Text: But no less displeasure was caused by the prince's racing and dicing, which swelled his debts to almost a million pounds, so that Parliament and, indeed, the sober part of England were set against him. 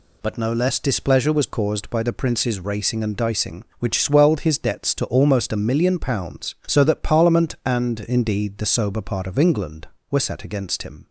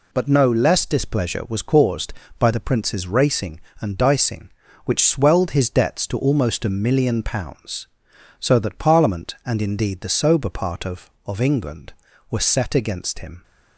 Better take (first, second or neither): first